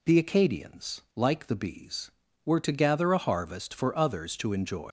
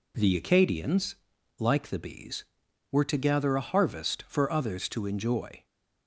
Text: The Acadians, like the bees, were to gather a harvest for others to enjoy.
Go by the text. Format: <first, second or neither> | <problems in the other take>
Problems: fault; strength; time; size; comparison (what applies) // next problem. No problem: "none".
second | leaves "enjoy" unfinished; at 4.8 s; 135 ms